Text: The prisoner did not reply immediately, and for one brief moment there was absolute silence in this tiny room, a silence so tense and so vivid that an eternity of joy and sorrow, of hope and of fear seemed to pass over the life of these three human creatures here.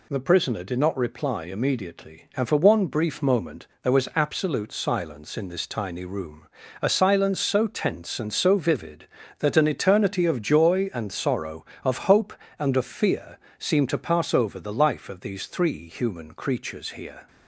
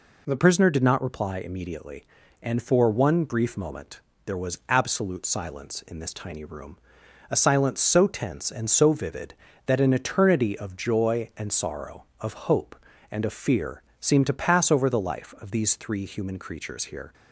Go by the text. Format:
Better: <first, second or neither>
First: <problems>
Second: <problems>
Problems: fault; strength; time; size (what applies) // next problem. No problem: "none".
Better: first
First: pauses between "moment" and "there"; slight; at 3.6 s; 0.16 s long // pauses between "fear" and "seemed"; slight; at 13.3 s; 0.20 s long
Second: changes voice at "prisoner"; from 0.3 s on; 16.8 s long // pauses between "moment" and "there"; slight; at 3.9 s; 0.26 s long // pauses between "fear" and "seemed"; slight; at 13.8 s; 0.16 s long